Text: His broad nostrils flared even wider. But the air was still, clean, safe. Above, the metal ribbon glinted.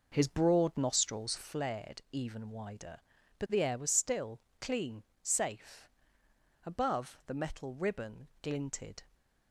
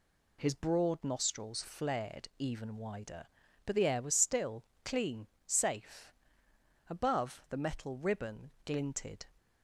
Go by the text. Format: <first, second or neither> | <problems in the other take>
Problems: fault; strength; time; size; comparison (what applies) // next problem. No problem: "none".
second | starts louder than the rest; noticeable; until 1.6 s; 5.5 dB